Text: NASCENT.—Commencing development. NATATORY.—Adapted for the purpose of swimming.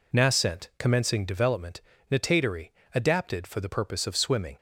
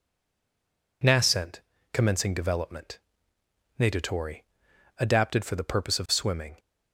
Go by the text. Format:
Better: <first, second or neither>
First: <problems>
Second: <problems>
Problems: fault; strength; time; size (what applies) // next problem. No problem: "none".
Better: first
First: none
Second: stays silent before the first word; until 1.0 s; 1.0 s long